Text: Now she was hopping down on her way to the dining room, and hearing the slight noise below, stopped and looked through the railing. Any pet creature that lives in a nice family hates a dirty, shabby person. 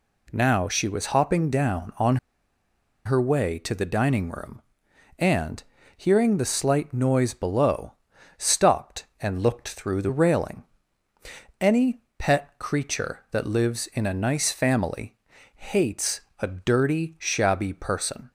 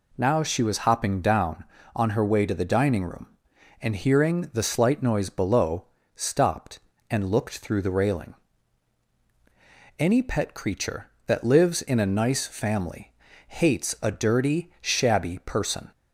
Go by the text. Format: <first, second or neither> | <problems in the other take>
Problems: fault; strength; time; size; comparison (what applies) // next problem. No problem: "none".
second | pauses between "on" and "her"; noticeable; at 2.1 s; 0.89 s long // pauses between "and" and "hearing"; slight; at 5.6 s; 0.34 s long // pauses between "Any" and "pet"; slight; at 12.0 s; 0.18 s long // pauses between "family" and "hates"; at 15.1 s; 0.40 s long; slight in the second // pauses between "hates" and "a"; slight; at 16.2 s; 0.20 s long